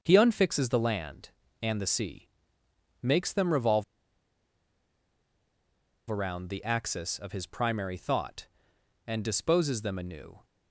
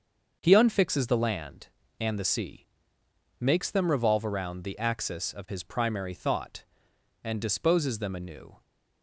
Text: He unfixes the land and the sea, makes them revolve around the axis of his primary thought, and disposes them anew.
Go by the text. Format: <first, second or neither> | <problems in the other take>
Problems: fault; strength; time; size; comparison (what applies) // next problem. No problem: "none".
second | starts louder than the rest; until 1.0 s; 6.5 dB; also in the second // pauses between "revolve" and "around"; strong; at 3.8 s; 2.2 s long